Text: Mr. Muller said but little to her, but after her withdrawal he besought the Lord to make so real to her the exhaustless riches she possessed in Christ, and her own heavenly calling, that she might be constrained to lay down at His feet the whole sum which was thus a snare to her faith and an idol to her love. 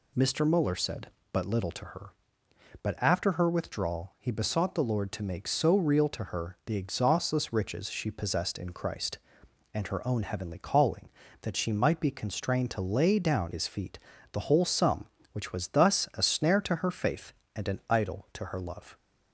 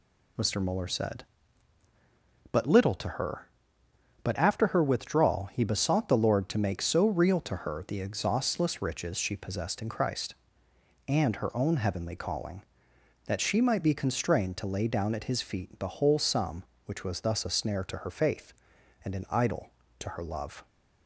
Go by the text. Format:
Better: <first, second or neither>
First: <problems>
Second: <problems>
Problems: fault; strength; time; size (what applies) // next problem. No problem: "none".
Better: second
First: skips "at"; at 13.5 s // pauses between "feet" and "the"; slight; at 13.9 s; 0.34 s long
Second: none